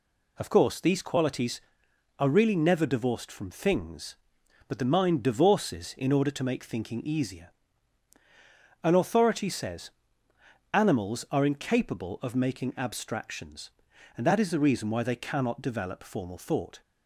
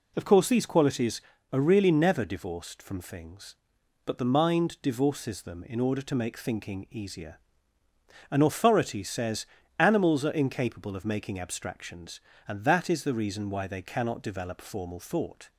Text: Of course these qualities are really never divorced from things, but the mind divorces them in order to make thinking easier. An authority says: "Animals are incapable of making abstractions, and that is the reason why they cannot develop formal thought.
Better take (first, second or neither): second